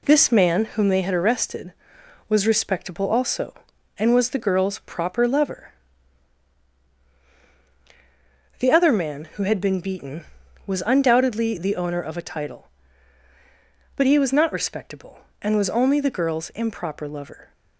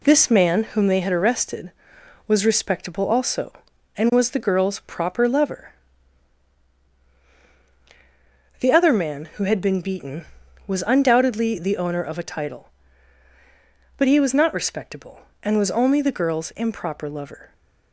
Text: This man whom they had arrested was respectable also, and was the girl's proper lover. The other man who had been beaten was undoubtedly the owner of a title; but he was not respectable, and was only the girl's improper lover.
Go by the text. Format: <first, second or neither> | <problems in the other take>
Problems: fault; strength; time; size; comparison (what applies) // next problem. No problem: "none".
neither | none